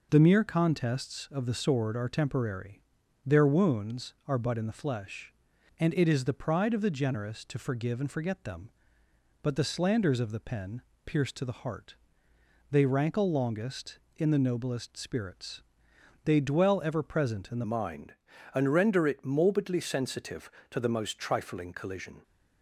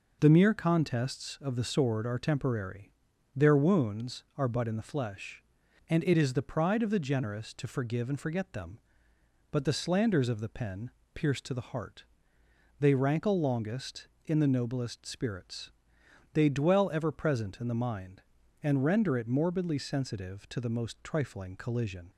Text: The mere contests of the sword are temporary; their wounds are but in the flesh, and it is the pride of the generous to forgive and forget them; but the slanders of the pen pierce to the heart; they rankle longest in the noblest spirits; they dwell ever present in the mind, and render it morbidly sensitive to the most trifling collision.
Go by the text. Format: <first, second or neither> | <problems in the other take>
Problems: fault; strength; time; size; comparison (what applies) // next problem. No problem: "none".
second | pauses between "pen" and "pierce"; slight; at 10.8 s; 0.24 s long; slight in the second // changes voice at "mind"; from 17.6 s on; 4.6 s long